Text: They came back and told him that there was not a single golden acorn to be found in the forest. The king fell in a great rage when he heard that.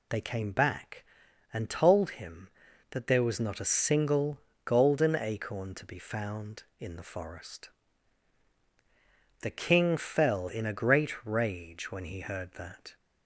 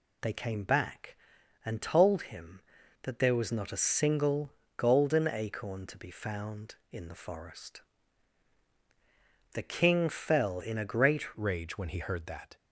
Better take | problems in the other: first | pauses between "single" and "golden"; slight; at 4.5 s; 0.24 s long; slight in the first // changes voice at "rage"; from 11.3 s on; 1.2 s long

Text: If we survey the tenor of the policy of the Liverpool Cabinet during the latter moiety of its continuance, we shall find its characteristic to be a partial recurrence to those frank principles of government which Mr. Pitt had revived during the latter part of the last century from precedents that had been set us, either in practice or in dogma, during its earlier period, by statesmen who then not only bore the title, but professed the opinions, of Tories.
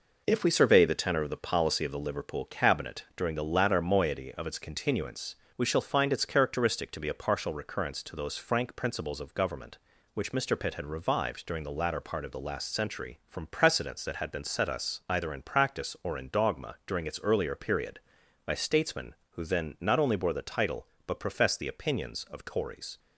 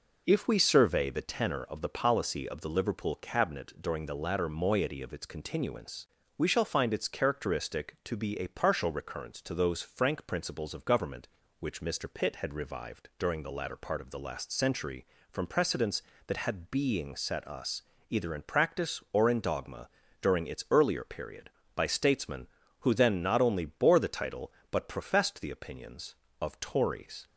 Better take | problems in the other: first | says "being" for "been"; at 16.6 s

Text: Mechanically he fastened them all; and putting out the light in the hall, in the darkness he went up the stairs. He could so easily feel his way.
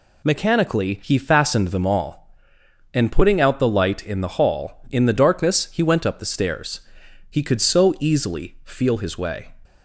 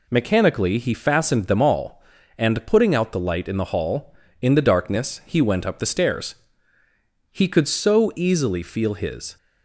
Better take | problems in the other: first | stops before "way"; at 9.3 s

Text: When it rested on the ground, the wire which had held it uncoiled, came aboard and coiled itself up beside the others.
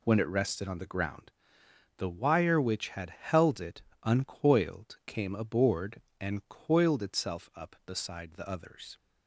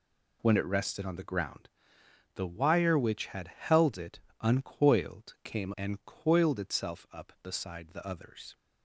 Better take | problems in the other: first | pauses between "it" and "uncoiled"; slight; at 4.1 s; 0.20 s long; slight in the first // skips "aboard"; at 5.7 s

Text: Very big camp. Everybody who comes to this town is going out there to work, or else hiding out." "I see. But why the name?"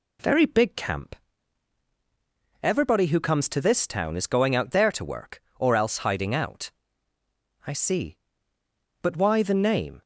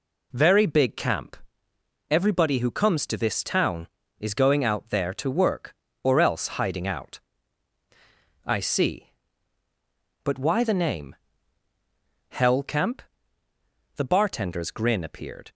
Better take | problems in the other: first | goes on to say "Hell Camp The bartender's grin appeared"; strong; from 12.2 s on; 3.2 s long

